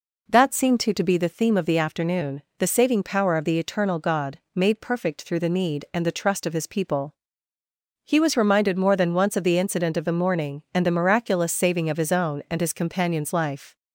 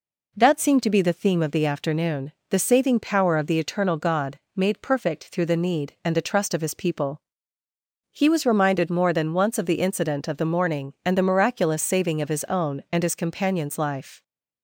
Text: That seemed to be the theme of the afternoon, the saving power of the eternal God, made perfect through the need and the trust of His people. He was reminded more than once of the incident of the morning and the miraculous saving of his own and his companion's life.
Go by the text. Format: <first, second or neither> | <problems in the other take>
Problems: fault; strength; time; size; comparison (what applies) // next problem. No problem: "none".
second | says "to" twice; at 0.9 s